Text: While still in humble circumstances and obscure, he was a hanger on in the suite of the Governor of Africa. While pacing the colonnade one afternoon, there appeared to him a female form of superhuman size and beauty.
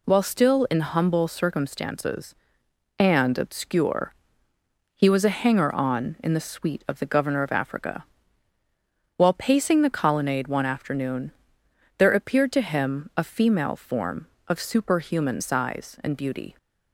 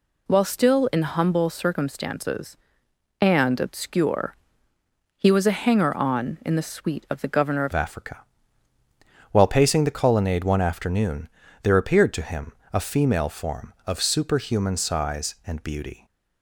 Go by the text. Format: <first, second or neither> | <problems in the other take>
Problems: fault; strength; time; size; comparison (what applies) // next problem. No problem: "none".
first | changes voice at "Africa"; from 7.7 s on; 8.3 s long // pauses between "him" and "a"; slight; at 12.5 s; 0.20 s long